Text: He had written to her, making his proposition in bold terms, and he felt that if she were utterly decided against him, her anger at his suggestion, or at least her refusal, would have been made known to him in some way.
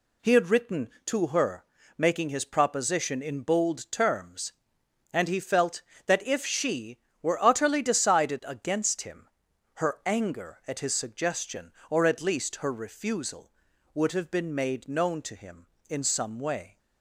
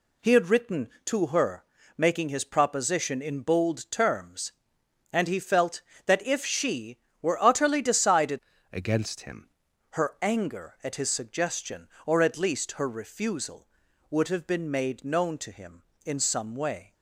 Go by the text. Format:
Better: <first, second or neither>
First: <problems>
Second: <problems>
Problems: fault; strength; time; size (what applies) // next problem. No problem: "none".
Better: first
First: none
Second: changes voice from "against" to "him"; from 8.7 to 9.5 s; 0.8 s long